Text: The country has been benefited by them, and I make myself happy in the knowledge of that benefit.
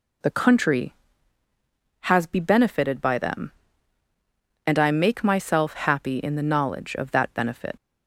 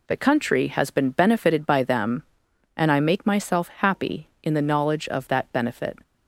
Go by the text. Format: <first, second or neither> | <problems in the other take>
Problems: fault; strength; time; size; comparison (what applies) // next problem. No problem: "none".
second | says "be" for "been"; at 2.2 s